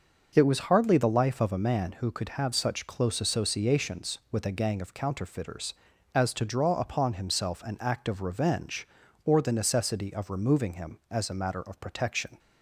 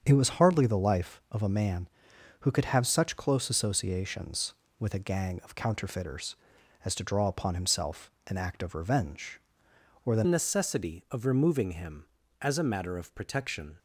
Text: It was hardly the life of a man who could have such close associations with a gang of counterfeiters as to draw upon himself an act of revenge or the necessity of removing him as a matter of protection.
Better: first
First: none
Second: starts louder than the rest; strong; until 1.0 s; 7.5 dB // pauses between "himself" and "an"; slight; at 8.0 s; 0.16 s long // changes voice at "necessity"; from 10.2 s on; 3.5 s long

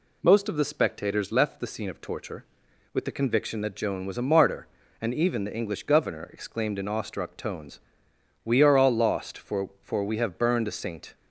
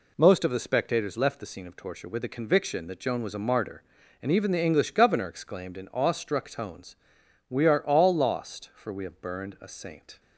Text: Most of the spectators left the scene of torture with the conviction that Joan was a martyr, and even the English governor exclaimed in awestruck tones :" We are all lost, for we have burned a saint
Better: second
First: says "for" twice; at 9.8 s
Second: none

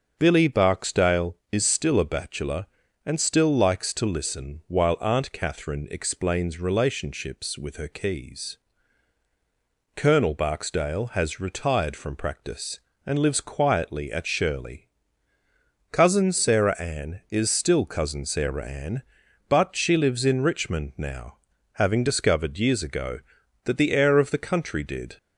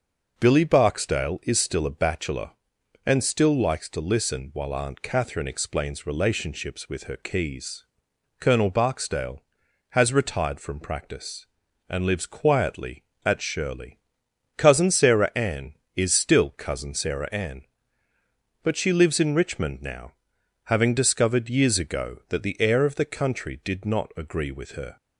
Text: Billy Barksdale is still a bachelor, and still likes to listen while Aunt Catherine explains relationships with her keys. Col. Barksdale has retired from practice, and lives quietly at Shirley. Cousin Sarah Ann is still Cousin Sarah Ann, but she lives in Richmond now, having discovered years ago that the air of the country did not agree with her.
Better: second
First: starts louder than the rest; until 1.1 s; 6.5 dB // stops before "not agree with her"; at 25.1 s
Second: none

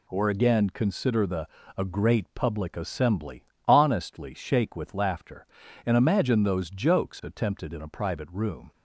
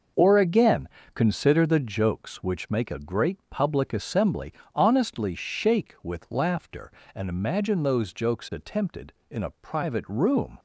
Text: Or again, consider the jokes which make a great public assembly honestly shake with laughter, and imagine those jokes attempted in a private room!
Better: second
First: skips "jokes which make"; at 1.6 s // pauses between "assembly" and "honestly"; slight; at 3.4 s; 0.22 s long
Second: pauses between "assembly" and "honestly"; slight; at 4.5 s; 0.20 s long

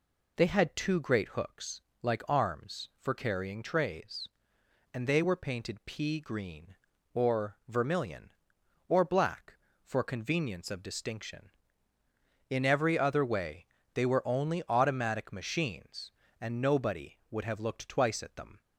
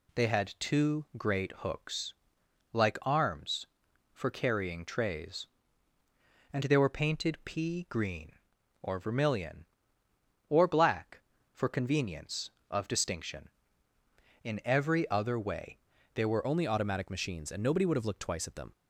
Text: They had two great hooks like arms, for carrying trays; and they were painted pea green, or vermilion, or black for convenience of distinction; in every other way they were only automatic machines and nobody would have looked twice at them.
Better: first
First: pauses between "hooks" and "like"; slight; at 1.8 s; 0.20 s long // pauses between "way" and "they"; slight; at 13.6 s; 0.28 s long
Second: pauses between "hooks" and "like"; noticeable; at 2.1 s; 0.58 s long // pauses between "way" and "they"; slight; at 15.7 s; 0.36 s long // changes voice at "only"; from 16.4 s on; 2.3 s long

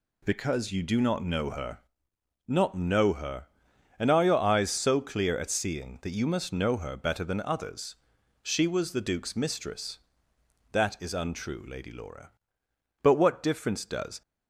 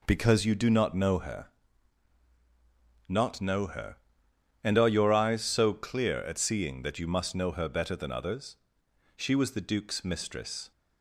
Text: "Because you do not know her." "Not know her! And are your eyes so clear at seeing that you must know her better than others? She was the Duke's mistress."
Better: second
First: goes on to say "That is untrue Lady Laura But what difference does"; strong; from 10.7 s on; 3.5 s long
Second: none

